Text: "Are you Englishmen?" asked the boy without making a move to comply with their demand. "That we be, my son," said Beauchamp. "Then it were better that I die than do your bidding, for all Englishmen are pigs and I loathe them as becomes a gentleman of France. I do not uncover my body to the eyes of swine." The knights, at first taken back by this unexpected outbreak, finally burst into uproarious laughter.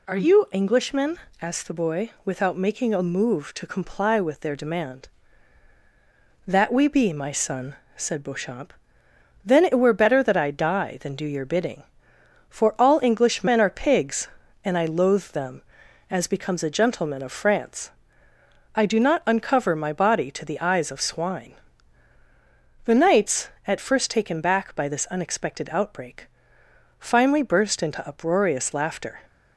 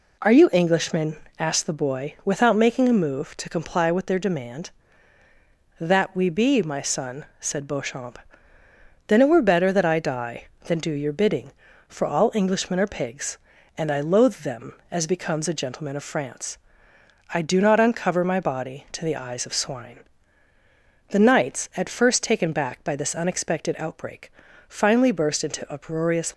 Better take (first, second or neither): first